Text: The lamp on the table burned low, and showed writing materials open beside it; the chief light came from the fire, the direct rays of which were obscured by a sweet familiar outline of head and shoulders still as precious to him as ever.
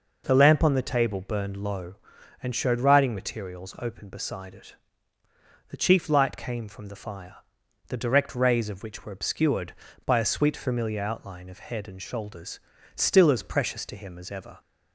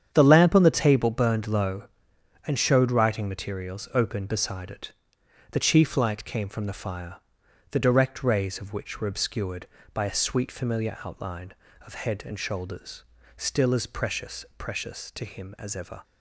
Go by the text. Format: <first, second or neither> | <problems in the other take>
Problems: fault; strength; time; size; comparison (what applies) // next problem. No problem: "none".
first | starts louder than the rest; strong; until 1.1 s; 8.5 dB // pauses between "shoulders" and "still"; slight; at 13.0 s; 0.34 s long; slight in the first // says "precious" twice; at 14.5 s